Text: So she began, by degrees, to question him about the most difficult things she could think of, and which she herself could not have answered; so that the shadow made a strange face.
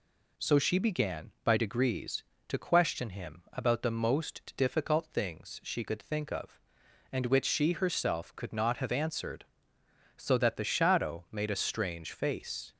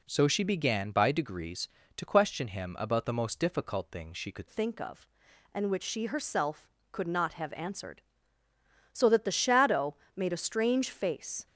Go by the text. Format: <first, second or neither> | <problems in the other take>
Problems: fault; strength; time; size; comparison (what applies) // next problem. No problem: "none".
first | changes voice at "think"; from 4.4 s on; 7.0 s long // pauses between "shadow" and "made"; slight; at 9.9 s; 0.20 s long